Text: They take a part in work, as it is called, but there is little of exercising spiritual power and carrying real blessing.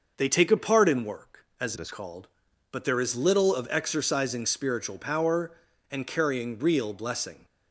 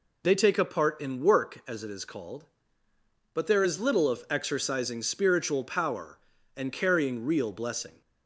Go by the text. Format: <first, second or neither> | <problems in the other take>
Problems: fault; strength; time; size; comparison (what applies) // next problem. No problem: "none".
second | starts louder than the rest; noticeable; until 1.1 s; 6 dB // changes voice from "it" to "is"; from 1.7 to 1.9 s; 0.2 s long